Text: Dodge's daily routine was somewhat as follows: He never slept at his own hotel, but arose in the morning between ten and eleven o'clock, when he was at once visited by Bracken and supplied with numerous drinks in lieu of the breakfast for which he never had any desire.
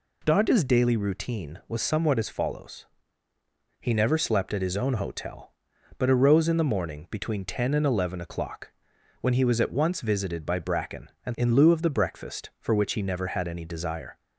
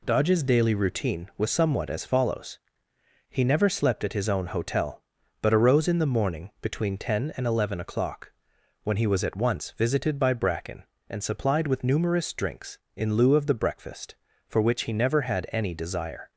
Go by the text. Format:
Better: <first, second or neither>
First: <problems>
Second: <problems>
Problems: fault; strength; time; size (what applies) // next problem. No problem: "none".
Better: second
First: skips "supplied with numerous drinks"; at 11.3 s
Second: none